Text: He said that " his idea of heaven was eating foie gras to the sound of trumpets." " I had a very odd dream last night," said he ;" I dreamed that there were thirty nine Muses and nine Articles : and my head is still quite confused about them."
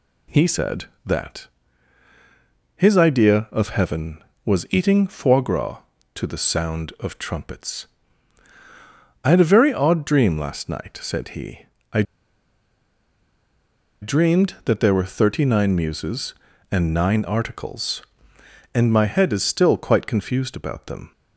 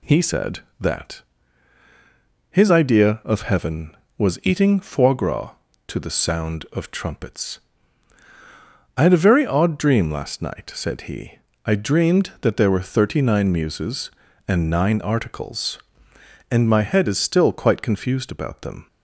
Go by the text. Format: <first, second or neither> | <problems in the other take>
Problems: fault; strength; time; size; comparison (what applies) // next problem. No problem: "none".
second | pauses between "I" and "dreamed"; strong; at 12.0 s; 1.9 s long